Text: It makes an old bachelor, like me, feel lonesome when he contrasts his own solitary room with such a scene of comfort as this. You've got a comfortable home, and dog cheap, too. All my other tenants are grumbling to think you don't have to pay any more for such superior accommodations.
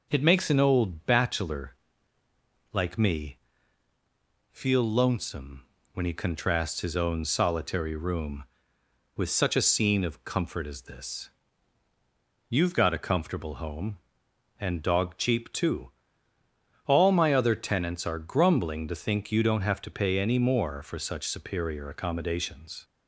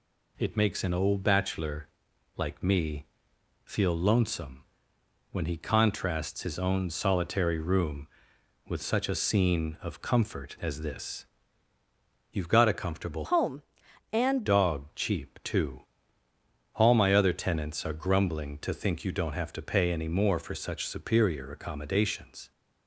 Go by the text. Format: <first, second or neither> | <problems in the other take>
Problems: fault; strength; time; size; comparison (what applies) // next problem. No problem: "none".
first | pauses between "lonesome" and "when"; noticeable; at 4.6 s; 0.68 s long; slight in the first // changes voice from "home" to "and"; from 13.2 to 14.4 s; 1.2 s long